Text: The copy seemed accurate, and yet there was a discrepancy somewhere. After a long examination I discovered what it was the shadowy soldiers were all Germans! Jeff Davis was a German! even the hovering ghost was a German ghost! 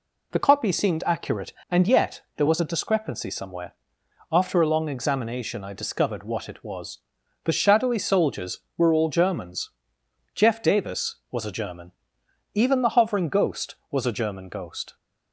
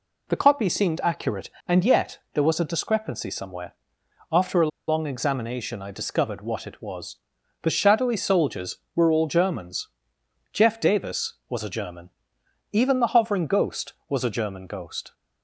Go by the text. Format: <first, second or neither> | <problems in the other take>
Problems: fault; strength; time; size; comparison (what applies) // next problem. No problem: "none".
first | pauses between "yet" and "there"; slight; at 2.1 s; 0.16 s long; slight in the first // pauses between "a" and "long"; slight; at 4.6 s; 0.20 s long // pauses between "was" and "the"; at 7.1 s; 0.44 s long; also in the first